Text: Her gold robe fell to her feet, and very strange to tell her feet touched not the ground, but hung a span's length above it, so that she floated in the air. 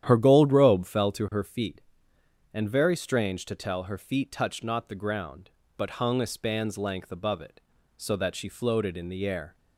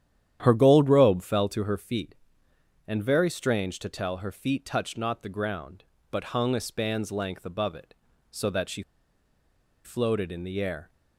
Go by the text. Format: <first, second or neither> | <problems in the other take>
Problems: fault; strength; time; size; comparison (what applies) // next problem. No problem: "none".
first | starts louder than the rest; strong; until 1.4 s; 10.5 dB; strong in the first // pauses between "she" and "floated"; at 8.8 s; 1.0 s long